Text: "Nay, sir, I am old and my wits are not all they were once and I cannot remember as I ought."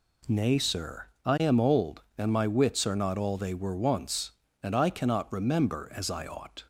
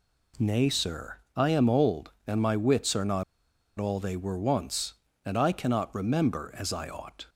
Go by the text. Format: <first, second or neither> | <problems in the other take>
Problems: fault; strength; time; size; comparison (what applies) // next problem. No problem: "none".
first | pauses between "not" and "all"; noticeable; at 3.2 s; 0.54 s long